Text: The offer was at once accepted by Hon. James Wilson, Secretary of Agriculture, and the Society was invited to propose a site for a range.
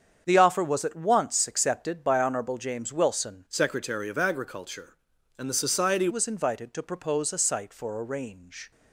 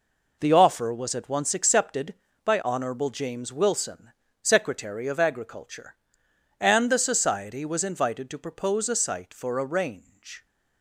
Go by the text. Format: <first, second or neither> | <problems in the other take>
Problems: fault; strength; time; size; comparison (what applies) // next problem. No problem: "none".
second | starts louder than the rest; strong; until 1.2 s; 7.5 dB // changes voice from "Secretary" to "Society"; from 3.4 to 6.0 s; 2.6 s long